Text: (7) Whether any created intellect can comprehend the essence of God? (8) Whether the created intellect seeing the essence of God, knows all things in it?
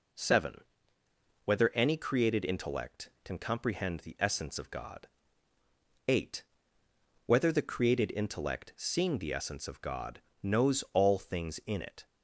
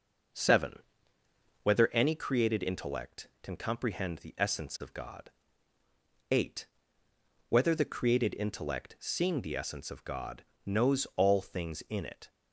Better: first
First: none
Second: starts louder than the rest; noticeable; until 2.1 s; 5.5 dB

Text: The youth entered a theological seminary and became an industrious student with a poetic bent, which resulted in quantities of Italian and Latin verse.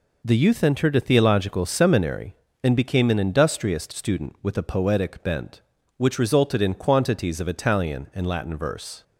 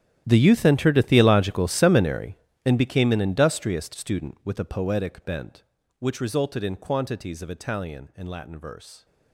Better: first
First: none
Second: gets quieter; strong; throughout; 18.5 dB

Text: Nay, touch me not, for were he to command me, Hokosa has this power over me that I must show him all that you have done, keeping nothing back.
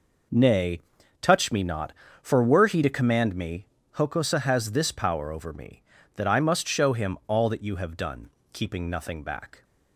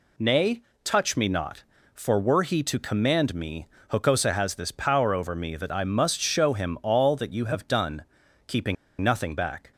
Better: first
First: none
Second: pauses between "keeping" and "nothing"; slight; at 8.7 s; 0.26 s long

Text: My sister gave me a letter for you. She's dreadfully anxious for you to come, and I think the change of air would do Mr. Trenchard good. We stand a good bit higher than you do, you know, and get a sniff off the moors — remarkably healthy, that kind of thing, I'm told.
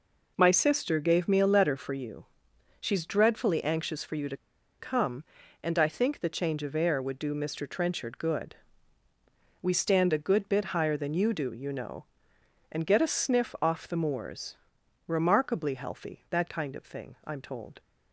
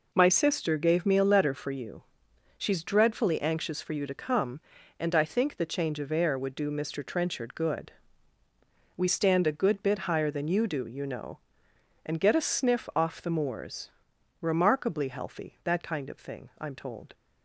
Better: second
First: pauses between "to" and "come"; at 4.3 s; 0.43 s long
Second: none

